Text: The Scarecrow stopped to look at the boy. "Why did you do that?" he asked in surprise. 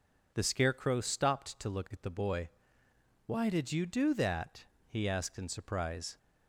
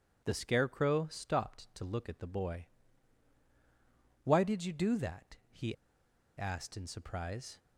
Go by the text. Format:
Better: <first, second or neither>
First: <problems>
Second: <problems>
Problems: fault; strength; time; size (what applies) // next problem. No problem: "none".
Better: first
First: none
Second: pauses between "he" and "asked"; noticeable; at 5.7 s; 0.63 s long